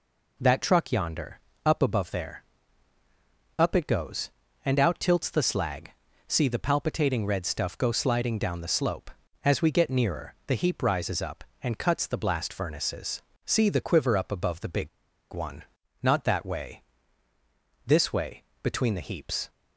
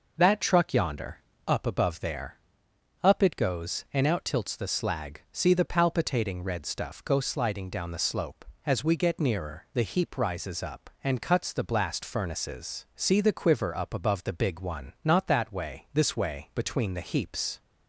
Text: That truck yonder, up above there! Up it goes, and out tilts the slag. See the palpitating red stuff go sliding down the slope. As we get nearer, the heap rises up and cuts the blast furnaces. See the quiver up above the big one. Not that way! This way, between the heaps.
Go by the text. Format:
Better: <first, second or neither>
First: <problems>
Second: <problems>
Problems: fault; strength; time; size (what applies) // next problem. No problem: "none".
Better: second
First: pauses between "big" and "one"; at 14.8 s; 0.44 s long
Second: none